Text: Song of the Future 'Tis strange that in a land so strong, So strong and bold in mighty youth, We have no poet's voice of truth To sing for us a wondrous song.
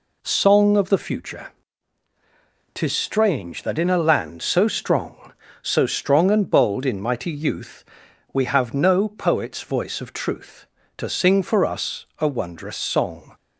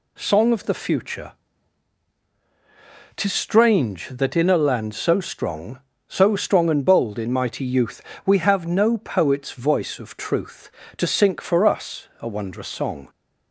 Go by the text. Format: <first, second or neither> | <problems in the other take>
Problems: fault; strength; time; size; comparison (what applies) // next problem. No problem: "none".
first | pauses between "Future" and "Tis"; strong; at 1.3 s; 1.8 s long; strong in the first // says "sink" for "sing"; at 11.0 s